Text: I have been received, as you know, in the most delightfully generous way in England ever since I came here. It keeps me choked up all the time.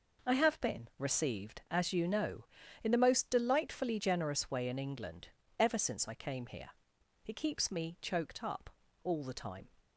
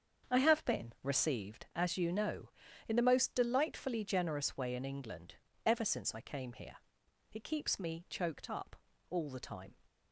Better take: first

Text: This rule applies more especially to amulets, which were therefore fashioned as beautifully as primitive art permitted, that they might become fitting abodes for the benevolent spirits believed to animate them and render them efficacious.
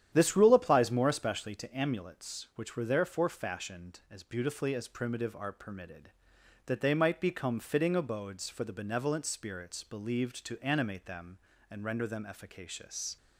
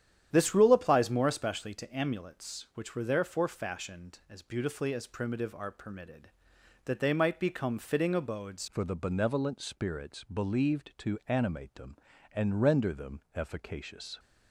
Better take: first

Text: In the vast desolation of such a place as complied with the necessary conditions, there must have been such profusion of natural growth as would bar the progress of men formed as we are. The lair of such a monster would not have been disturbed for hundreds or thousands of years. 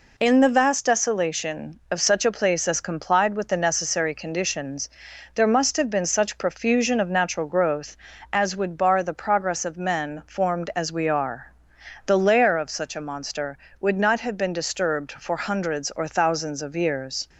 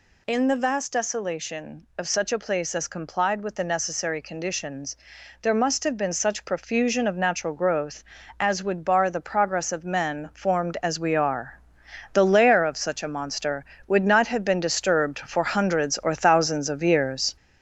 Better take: first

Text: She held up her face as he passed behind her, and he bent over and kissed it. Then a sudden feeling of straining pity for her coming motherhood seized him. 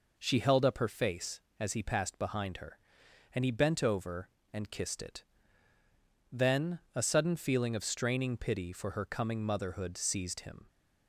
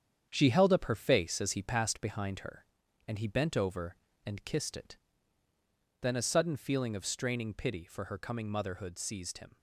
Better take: first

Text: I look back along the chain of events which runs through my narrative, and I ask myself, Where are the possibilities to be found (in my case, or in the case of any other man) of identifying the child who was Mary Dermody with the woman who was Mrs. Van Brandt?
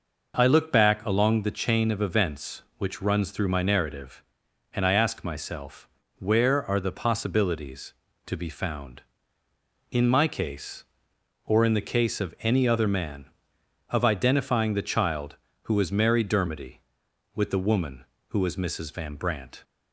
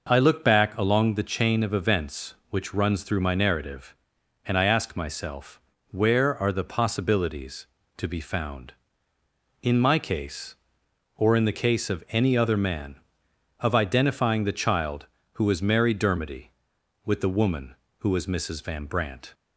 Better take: neither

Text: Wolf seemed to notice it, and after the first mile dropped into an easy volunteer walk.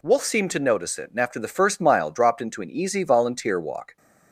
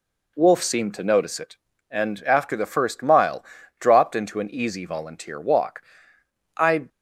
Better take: first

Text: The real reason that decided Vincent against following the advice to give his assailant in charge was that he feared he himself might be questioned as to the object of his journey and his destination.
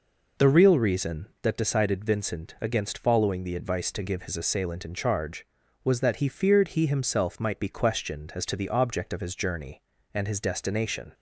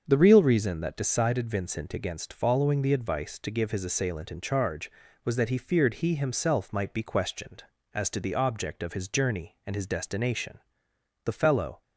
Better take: first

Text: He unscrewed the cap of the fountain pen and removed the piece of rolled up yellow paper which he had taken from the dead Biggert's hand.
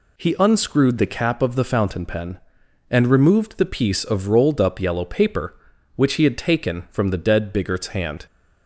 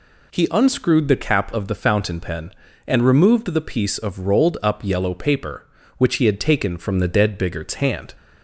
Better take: neither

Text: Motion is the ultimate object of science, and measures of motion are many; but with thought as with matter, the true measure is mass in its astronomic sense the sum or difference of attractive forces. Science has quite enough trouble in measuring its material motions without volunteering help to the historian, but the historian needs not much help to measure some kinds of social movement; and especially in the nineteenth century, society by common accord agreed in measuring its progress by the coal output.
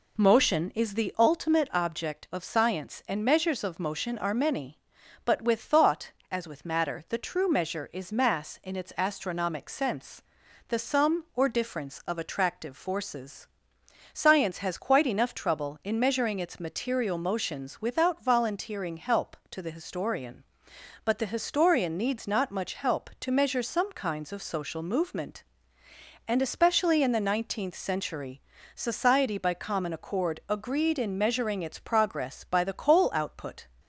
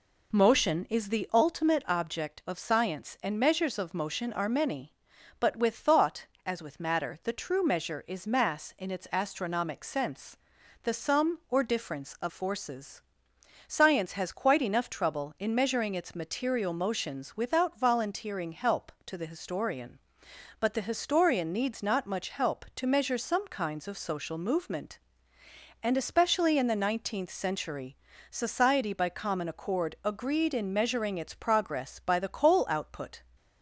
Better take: first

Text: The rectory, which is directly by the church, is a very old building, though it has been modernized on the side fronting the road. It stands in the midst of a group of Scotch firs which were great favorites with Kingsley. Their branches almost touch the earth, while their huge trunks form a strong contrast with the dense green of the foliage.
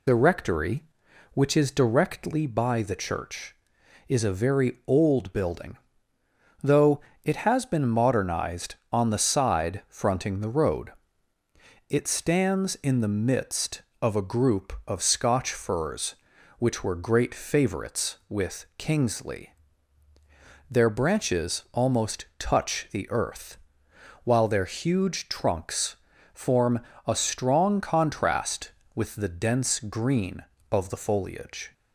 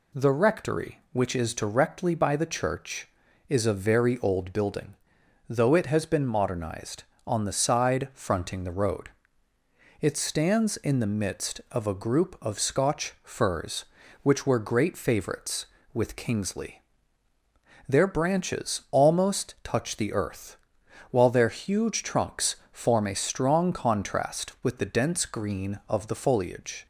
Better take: second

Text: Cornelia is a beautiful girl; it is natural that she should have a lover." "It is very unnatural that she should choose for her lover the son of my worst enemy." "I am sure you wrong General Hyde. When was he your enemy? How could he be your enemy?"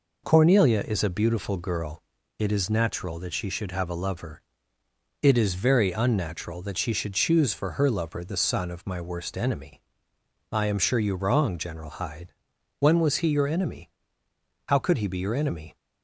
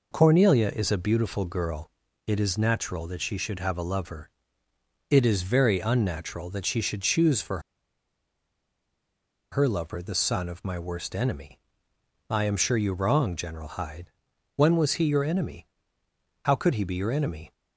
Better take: first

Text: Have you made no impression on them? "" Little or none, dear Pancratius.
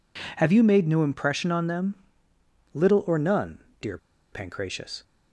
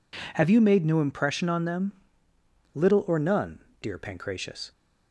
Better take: second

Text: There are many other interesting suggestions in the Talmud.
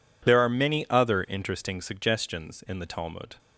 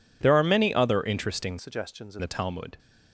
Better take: first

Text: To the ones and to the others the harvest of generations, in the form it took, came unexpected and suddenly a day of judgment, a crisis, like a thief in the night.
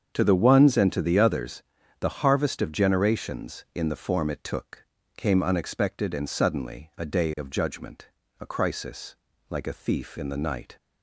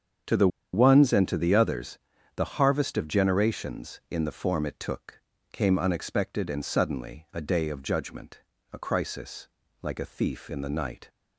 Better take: first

